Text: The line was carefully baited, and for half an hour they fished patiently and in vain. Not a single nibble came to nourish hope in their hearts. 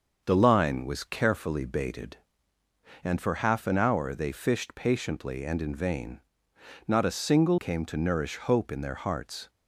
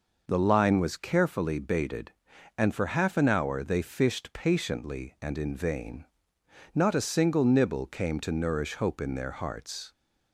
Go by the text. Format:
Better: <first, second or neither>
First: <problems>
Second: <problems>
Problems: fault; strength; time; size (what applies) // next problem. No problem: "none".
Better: second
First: starts louder than the rest; until 1.2 s; 6 dB // skips "nibble"; at 7.5 s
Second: none